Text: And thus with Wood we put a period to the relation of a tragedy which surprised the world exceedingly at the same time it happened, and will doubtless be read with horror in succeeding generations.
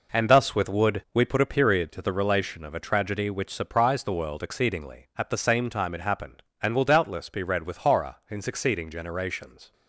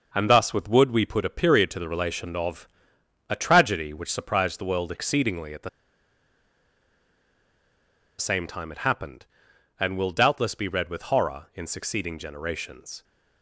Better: first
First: none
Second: pauses between "of" and "a"; noticeable; at 2.6 s; 0.62 s long // pauses between "the" and "same"; strong; at 5.6 s; 2.4 s long

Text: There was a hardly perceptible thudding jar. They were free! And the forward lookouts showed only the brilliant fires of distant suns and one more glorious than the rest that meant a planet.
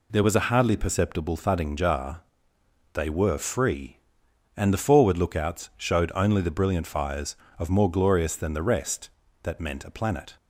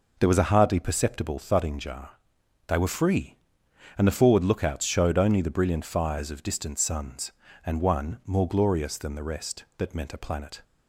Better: second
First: skips "distant suns and one"; at 7.7 s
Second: none

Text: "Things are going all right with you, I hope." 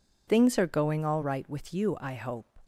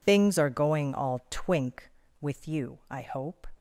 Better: first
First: none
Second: says "twink" for "right"; at 1.2 s

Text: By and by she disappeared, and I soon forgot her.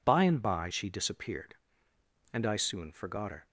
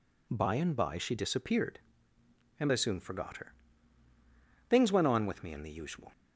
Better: first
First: none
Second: goes on to say "Things went on with me in the usual"; from 4.6 s on; 1.4 s long

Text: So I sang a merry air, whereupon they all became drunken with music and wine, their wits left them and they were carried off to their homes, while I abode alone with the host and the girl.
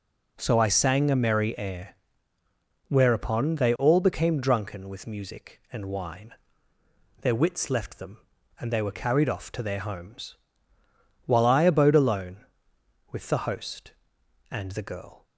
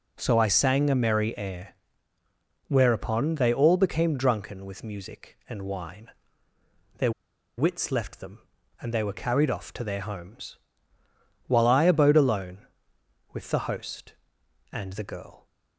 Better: first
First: none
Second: pauses between "their" and "wits"; noticeable; at 7.1 s; 0.47 s long

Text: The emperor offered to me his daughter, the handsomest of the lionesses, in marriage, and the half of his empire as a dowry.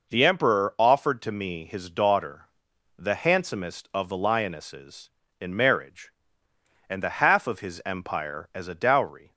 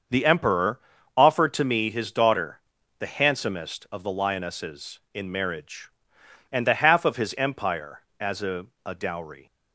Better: first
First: none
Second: starts louder than the rest; until 1.4 s; 6.5 dB // pauses between "emperor" and "offered"; slight; at 0.7 s; 0.36 s long // says "a" twice; at 8.8 s

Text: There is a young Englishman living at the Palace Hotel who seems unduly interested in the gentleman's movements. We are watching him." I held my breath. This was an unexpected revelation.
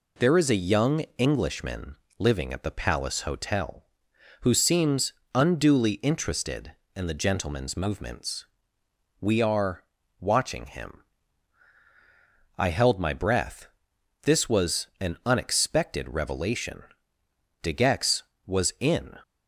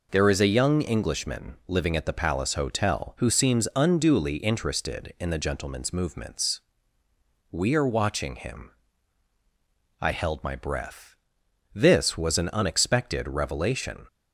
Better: second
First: pauses between "young" and "Englishman"; slight; at 1.0 s; 0.18 s long // pauses between "Englishman" and "living"; slight; at 1.9 s; 0.22 s long // pauses between "seems" and "unduly"; slight; at 5.1 s; 0.22 s long // pauses between "are" and "watching"; slight; at 9.8 s; 0.36 s long // goes on to say "De Gex was in"; from 17.6 s on; 1.5 s long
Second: none

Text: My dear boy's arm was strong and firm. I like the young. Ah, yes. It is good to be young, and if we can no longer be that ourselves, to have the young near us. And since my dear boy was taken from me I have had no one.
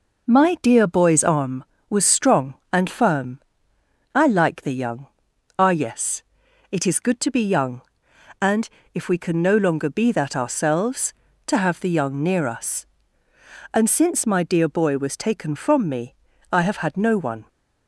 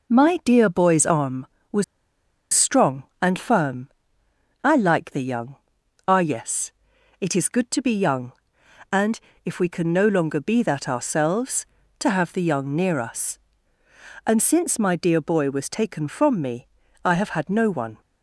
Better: first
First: pauses between "and" and "if"; slight; at 8.6 s; 0.26 s long // pauses between "me" and "I"; slight; at 16.1 s; 0.36 s long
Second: pauses between "was" and "strong"; noticeable; at 1.8 s; 0.69 s long // pauses between "and" and "if"; slight; at 9.1 s; 0.26 s long // pauses between "me" and "I"; slight; at 16.6 s; 0.36 s long

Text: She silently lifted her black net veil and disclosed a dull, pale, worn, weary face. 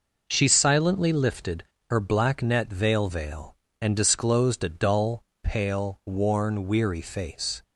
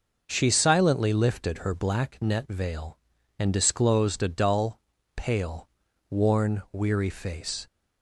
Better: second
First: pauses between "lifted" and "her"; slight; at 1.6 s; 0.26 s long // says "veil" twice; at 3.0 s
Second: none

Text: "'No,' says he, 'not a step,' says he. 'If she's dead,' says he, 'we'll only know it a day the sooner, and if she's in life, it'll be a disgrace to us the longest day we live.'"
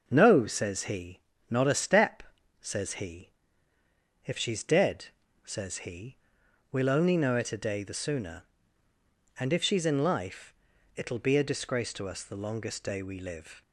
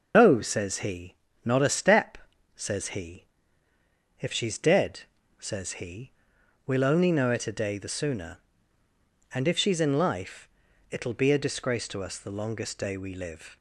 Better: first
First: none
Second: loses the start of "No"; at 0.1 s; 120 ms // starts louder than the rest; noticeable; until 1.1 s; 6 dB

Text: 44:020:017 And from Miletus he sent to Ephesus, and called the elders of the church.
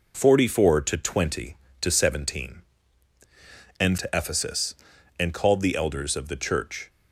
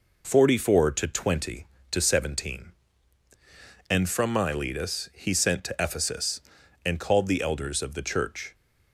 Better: second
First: skips "from Miletus he sent"; at 3.9 s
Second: none

